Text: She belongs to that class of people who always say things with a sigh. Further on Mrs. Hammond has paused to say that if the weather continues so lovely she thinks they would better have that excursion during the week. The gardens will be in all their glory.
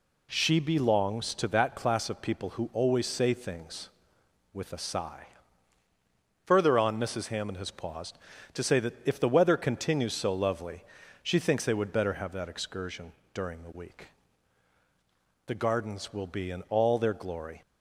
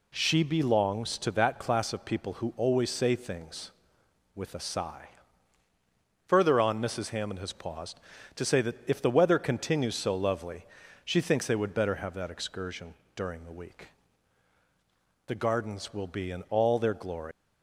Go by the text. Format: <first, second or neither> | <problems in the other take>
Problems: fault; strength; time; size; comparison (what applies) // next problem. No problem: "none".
first | pauses between "lovely" and "she"; at 10.6 s; 0.40 s long; also in the first // pauses between "excursion" and "during"; slight; at 12.9 s; 0.22 s long; slight in the first // leaves "glory" unfinished; at 17.3 s; 100 ms